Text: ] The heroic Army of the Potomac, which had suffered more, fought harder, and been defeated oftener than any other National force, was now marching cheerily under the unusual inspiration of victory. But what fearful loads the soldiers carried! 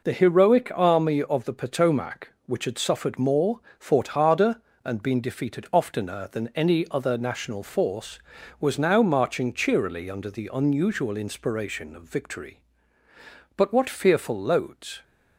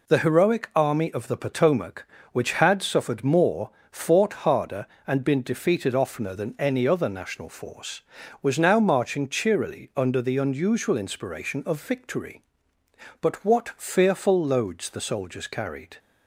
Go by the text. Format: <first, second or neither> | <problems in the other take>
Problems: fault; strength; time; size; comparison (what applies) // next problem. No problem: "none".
second | stops before "the soldiers carried"; at 15.0 s